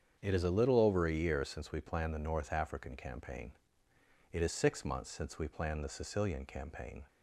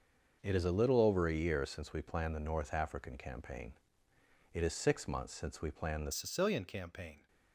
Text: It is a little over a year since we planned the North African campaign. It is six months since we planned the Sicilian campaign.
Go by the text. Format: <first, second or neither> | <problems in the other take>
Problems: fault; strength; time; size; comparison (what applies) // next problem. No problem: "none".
first | starts louder than the rest; until 1.4 s; 6.5 dB; strong in the first // changes voice at "Sicilian"; from 6.1 s on; 1.1 s long